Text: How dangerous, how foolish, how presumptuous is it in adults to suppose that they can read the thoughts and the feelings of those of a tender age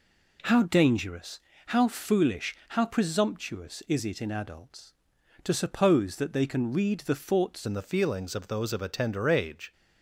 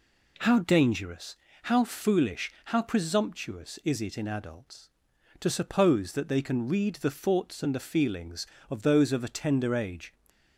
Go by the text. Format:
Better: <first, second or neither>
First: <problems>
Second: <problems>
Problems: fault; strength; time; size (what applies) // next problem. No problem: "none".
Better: second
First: changes voice at "and"; from 7.6 s on; 2.1 s long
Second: none